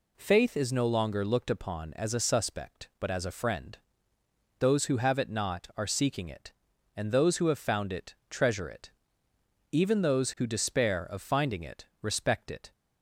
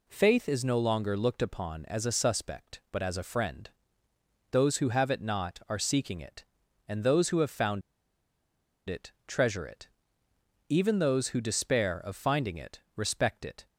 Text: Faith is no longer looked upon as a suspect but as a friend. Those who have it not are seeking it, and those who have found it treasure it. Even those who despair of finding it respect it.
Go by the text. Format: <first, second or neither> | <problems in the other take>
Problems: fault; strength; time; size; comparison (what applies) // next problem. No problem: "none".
first | pauses between "found" and "it"; at 7.8 s; 1.0 s long // pauses between "it" and "respect"; slight; at 12.8 s; 0.16 s long; slight in the first